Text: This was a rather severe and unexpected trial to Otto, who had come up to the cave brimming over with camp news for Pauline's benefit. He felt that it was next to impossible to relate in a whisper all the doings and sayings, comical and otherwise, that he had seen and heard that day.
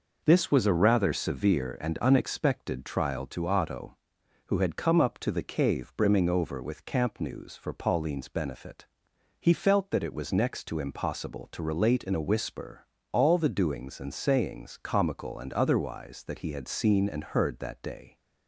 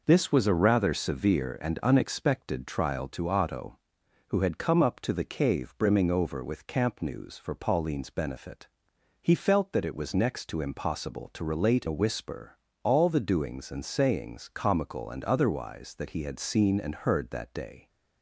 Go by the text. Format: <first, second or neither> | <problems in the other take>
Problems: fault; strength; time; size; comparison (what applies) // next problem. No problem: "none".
first | skips "in"; at 11.8 s // pauses between "whisper" and "all"; slight; at 12.5 s; 0.28 s long; slight in the first